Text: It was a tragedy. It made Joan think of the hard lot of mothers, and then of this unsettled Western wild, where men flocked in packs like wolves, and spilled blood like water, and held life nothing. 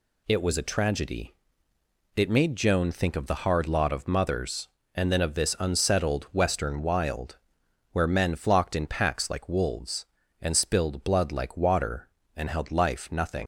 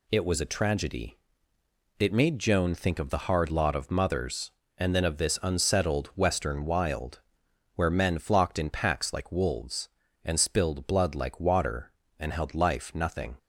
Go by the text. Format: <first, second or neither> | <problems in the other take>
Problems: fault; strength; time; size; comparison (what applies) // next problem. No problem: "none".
second | leaves "nothing" unfinished; at 13.4 s; 85 ms